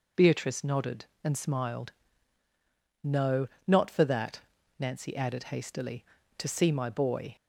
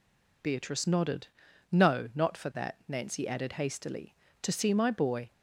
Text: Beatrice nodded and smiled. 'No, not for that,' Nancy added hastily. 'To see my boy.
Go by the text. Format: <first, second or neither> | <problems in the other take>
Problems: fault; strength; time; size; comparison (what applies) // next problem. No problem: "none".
first | skips "and smiled"; at 1.4 s